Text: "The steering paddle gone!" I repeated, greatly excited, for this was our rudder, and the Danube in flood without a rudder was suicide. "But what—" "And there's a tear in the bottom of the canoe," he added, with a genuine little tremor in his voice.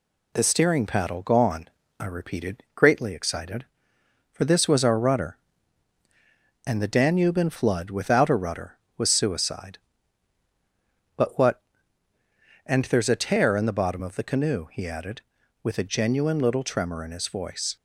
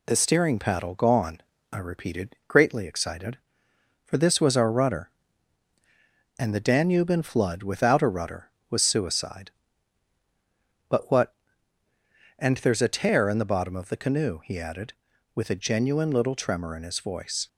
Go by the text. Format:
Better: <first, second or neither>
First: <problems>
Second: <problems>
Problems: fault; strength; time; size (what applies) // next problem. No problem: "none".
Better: neither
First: none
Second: none